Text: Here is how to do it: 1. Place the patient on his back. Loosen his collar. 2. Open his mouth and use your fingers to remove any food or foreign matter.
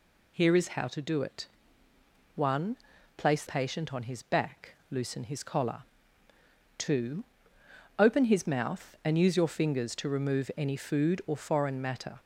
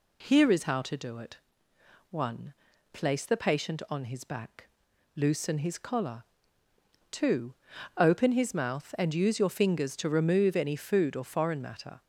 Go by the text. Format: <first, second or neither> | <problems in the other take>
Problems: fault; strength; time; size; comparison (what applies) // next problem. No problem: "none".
second | skips "the"; at 3.4 s